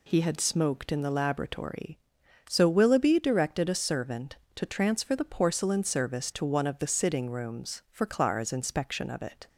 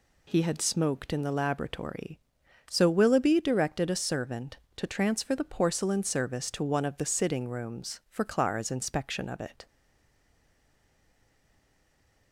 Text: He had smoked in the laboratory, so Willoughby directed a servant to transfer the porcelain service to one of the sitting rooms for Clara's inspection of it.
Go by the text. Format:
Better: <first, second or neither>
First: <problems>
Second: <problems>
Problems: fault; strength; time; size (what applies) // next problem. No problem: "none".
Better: first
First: none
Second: stays silent after the last word; strong; from 9.6 s on; 2.7 s long